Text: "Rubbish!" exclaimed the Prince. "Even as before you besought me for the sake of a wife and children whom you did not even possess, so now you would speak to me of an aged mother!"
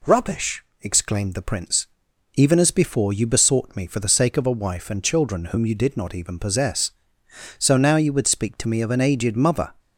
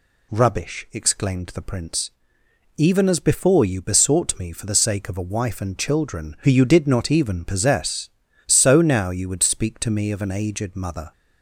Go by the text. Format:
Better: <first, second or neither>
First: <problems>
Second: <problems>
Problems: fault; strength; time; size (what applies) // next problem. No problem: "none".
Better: first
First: none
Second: says "who" for "whom"; at 6.3 s